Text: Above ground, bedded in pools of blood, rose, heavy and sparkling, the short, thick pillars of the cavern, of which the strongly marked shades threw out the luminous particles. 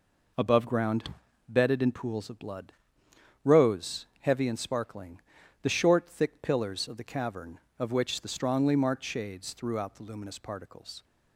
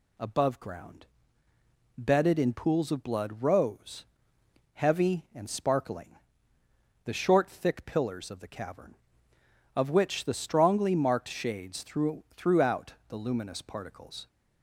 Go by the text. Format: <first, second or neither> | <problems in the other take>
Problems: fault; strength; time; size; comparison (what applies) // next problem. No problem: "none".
first | says "threw" twice; at 12.3 s // pauses between "out" and "the"; slight; at 12.9 s; 0.16 s long